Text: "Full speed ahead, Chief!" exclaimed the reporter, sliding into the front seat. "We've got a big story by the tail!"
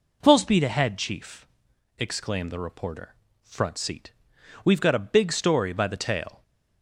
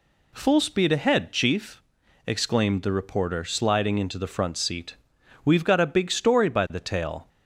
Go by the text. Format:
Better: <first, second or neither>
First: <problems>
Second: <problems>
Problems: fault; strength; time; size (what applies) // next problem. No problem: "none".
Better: second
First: skips "sliding into the"; at 3.2 s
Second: none